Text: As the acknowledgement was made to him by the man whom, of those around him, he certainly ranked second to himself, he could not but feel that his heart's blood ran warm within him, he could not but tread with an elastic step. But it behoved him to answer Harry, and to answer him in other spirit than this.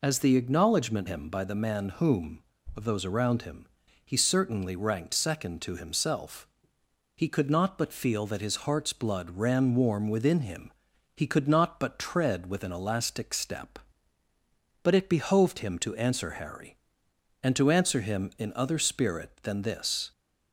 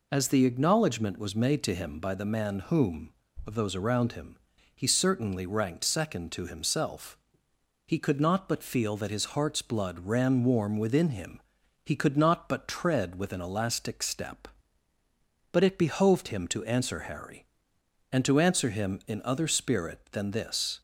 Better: second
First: skips "was made to"; at 1.0 s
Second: none

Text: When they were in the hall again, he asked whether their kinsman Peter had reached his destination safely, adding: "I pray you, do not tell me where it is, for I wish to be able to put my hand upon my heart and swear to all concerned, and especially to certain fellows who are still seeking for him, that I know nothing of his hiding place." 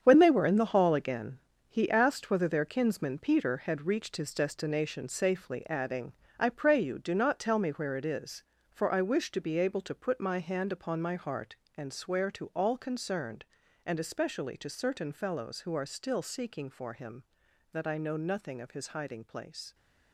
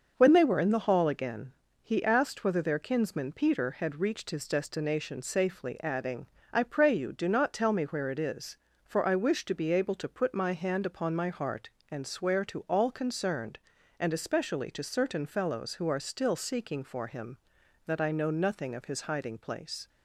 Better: second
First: gets quieter; strong; throughout; 9.5 dB // starts louder than the rest; strong; until 1.0 s; 8 dB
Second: starts louder than the rest; until 1.1 s; 6 dB

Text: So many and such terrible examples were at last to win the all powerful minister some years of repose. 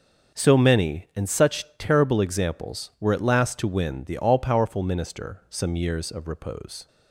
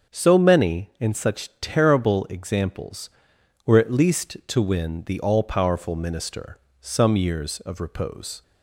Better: first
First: none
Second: starts louder than the rest; until 1.2 s; 7 dB // says "least" for "last"; at 3.9 s // pauses between "minister" and "some"; slight; at 6.5 s; 0.22 s long

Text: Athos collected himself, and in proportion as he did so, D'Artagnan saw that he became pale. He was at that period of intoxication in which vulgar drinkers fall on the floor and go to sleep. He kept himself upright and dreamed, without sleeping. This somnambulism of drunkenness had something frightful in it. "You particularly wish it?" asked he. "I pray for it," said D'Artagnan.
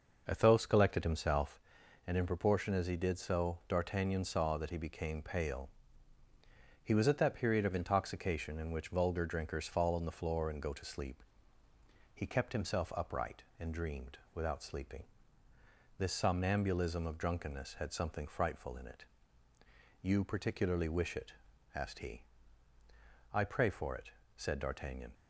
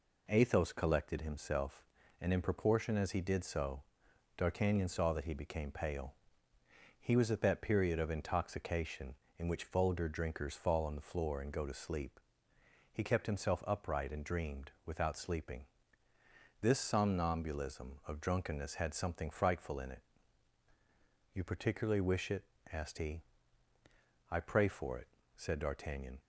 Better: second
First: starts louder than the rest; noticeable; until 1.6 s; 5.5 dB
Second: none

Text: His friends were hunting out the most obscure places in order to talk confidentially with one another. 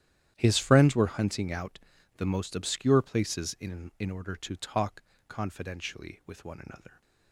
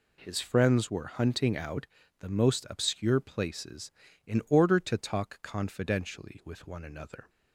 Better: second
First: starts louder than the rest; strong; until 1.3 s; 11 dB // pauses between "out" and "the"; at 1.7 s; 0.38 s long // says "in" twice; at 3.9 s // pauses between "talk" and "confidentially"; slight; at 5.0 s; 0.26 s long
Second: pauses between "out" and "the"; slight; at 1.8 s; 0.34 s long

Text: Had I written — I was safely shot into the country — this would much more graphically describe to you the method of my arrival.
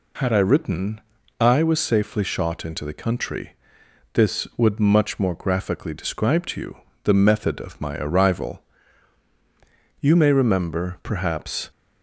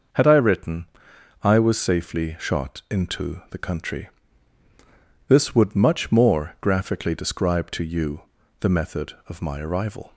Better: second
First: pauses between "you" and "the"; slight; at 6.7 s; 0.28 s long // goes on to say "You may remember perhaps"; strong; from 10.0 s on; 1.6 s long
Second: pauses between "you" and "the"; at 8.2 s; 0.38 s long

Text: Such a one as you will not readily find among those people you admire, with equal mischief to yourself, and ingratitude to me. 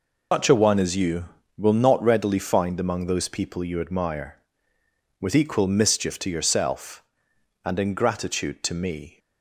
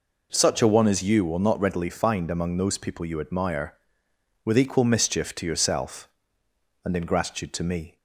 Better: second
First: loses the start of "Such"; at 0.3 s; 150 ms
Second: none

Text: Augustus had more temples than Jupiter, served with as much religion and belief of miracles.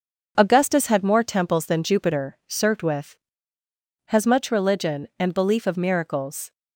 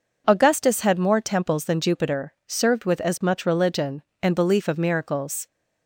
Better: second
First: starts louder than the rest; until 1.3 s; 6.5 dB // says "has" for "as"; at 4.0 s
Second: none

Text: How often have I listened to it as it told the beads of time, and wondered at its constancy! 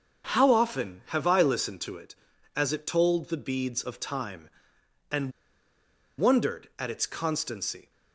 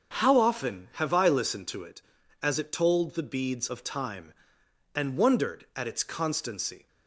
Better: second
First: starts louder than the rest; until 1.3 s; 7 dB // pauses between "and" and "wondered"; noticeable; at 5.3 s; 0.86 s long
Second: starts louder than the rest; until 1.2 s; 7 dB

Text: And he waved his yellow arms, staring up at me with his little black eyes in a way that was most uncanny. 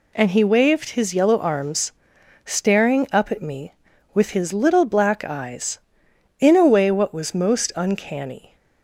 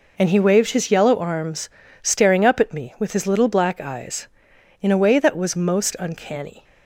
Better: second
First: says "what" for "that"; at 6.9 s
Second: none

